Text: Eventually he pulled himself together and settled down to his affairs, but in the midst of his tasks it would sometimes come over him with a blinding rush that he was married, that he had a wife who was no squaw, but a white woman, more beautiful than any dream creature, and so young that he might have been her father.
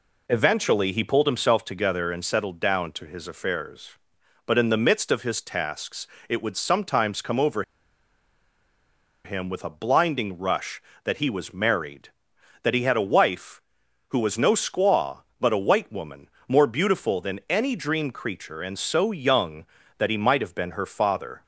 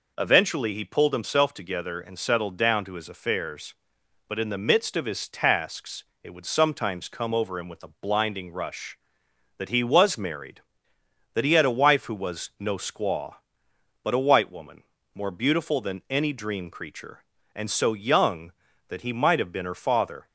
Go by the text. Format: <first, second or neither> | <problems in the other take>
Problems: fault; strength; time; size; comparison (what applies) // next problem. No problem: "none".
second | pauses between "tasks" and "it"; slight; at 6.0 s; 0.22 s long; slight in the second // pauses between "over" and "him"; strong; at 7.6 s; 1.6 s long